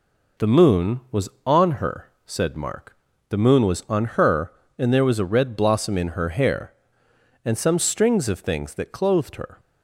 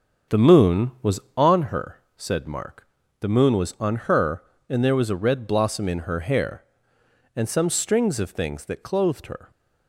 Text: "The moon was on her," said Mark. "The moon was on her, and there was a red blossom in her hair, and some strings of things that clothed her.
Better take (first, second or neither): first